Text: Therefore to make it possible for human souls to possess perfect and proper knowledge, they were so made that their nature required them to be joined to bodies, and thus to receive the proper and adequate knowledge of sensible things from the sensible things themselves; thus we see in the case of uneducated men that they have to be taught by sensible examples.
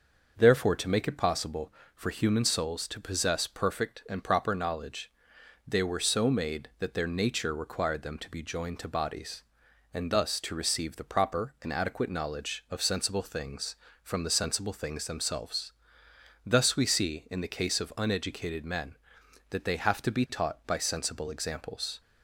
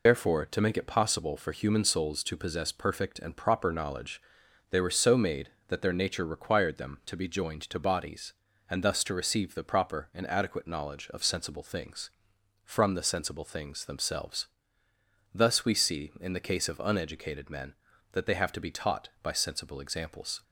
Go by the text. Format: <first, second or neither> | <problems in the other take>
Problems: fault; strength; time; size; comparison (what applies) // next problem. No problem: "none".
first | loses the start of "Therefore"; at 0.0 s; 75 ms